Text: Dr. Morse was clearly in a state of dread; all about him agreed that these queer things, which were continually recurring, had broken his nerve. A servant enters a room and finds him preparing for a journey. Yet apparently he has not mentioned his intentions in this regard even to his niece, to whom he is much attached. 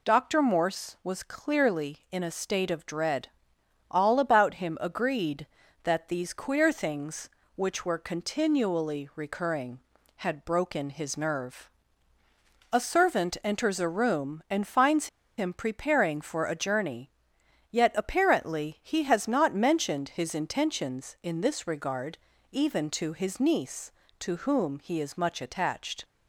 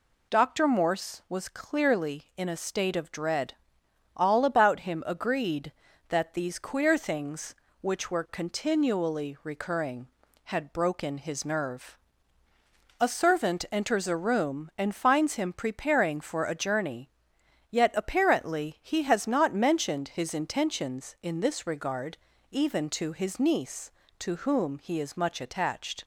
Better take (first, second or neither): second